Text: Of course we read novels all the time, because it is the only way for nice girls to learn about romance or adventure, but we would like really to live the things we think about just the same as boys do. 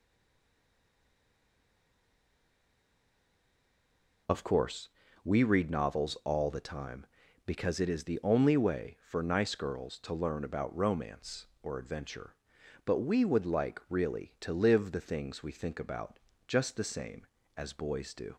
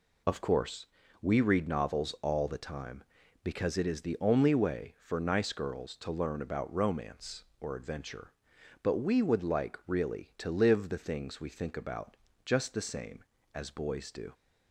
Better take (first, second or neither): second